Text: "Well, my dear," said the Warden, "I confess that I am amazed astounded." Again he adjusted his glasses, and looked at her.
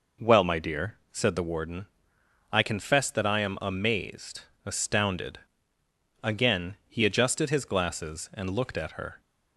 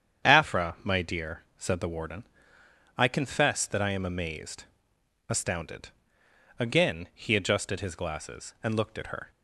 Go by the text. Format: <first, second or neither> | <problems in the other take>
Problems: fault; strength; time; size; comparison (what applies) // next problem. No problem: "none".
first | starts louder than the rest; strong; until 1.3 s; 8.5 dB // says "Afra" for "Well"; at 0.2 s // pauses between "amazed" and "astounded"; noticeable; at 4.6 s; 0.62 s long; slight in the first